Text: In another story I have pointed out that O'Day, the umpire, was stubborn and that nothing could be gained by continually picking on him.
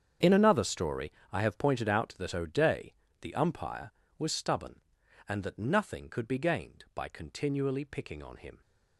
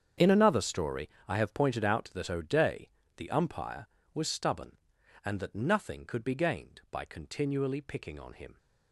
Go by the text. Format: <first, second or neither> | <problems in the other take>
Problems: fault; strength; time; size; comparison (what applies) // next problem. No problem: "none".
neither | starts louder than the rest; strong; the same in both // pauses between "story" and "I"; slight; the same in both